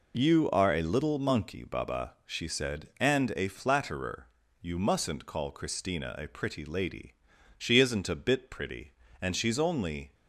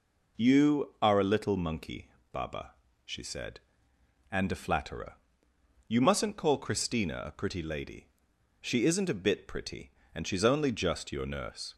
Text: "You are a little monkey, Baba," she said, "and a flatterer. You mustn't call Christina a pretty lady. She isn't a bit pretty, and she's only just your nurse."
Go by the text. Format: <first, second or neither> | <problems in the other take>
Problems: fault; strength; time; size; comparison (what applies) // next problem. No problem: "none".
second | stops before "just your nurse"; at 10.1 s